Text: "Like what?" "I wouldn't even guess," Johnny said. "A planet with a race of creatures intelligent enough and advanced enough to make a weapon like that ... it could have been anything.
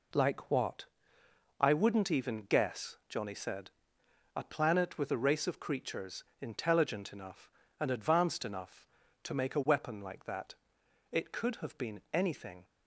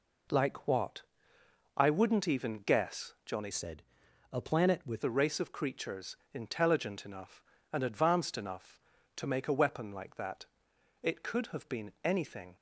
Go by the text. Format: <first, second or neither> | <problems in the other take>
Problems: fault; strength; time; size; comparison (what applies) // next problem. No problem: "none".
first | changes voice from "said" to "with"; from 3.5 to 5.0 s; 1.5 s long // pauses between "creatures" and "intelligent"; slight; at 6.1 s; 0.18 s long; slight in the first